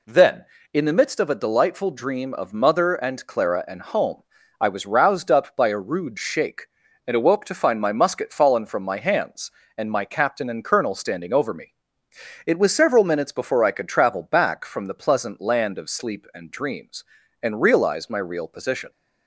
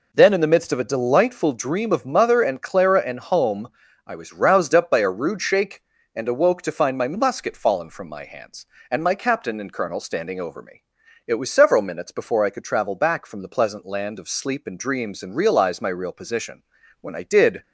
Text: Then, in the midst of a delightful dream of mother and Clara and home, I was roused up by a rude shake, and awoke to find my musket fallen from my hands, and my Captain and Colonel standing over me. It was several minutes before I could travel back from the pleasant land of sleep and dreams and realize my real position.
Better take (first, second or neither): first